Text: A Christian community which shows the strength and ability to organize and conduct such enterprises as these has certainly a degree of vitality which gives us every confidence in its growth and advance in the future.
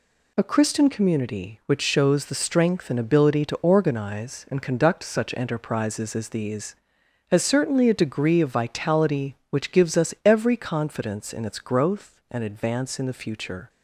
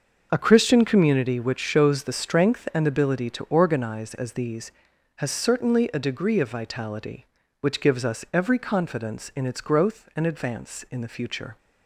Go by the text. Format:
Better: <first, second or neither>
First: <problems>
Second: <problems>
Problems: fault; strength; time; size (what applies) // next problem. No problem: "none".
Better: first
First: none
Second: starts louder than the rest; until 1.3 s; 6 dB // skips "and conduct such enterprises"; at 4.1 s